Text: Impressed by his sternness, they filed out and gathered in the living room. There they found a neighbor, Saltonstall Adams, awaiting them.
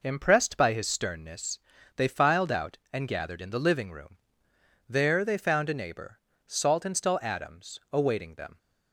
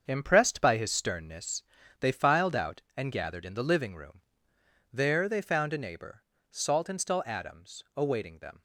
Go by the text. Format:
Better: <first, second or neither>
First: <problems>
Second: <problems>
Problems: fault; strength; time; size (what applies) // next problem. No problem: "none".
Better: first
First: none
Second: gets quieter; strong; throughout; 8.5 dB